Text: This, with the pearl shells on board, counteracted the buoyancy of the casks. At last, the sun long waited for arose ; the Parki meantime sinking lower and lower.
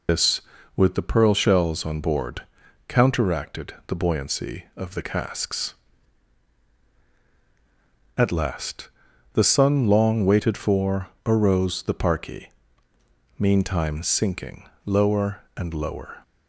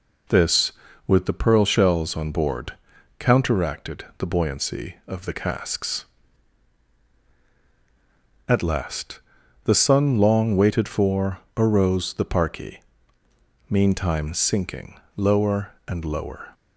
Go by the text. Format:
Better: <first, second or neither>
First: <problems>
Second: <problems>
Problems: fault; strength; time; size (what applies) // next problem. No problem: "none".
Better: second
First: loses the start of "This"; at 0.0 s; 105 ms // pauses between "for" and "arose"; slight; at 11.0 s; 0.16 s long // pauses between "Parki" and "meantime"; noticeable; at 12.5 s; 0.88 s long // pauses between "sinking" and "lower"; slight; at 14.6 s; 0.20 s long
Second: pauses between "for" and "arose"; slight; at 11.3 s; 0.16 s long // pauses between "Parki" and "meantime"; noticeable; at 12.8 s; 0.88 s long // pauses between "sinking" and "lower"; slight; at 14.9 s; 0.20 s long